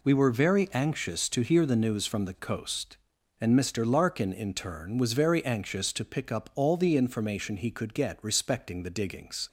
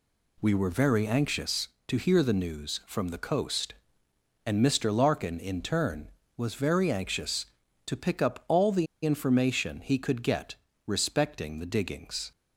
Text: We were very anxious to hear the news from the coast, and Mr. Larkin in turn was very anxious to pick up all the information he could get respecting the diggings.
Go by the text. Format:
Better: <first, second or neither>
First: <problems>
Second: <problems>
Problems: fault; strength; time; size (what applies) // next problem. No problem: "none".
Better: first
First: none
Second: pauses between "the" and "information"; slight; at 8.8 s; 0.19 s long // pauses between "get" and "respecting"; slight; at 10.5 s; 0.32 s long